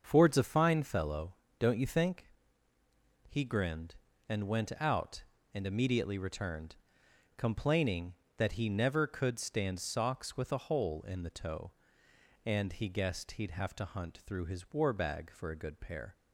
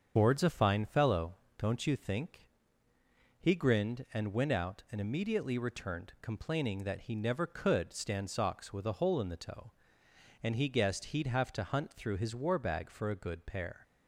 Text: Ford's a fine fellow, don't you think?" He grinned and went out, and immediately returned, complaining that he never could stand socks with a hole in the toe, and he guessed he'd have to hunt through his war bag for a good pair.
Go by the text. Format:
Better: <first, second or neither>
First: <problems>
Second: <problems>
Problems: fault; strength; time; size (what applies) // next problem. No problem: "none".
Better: first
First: starts louder than the rest; until 1.0 s; 6.5 dB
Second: loses the start of "Ford's"; at 0.1 s; 115 ms // starts louder than the rest; until 1.1 s; 7 dB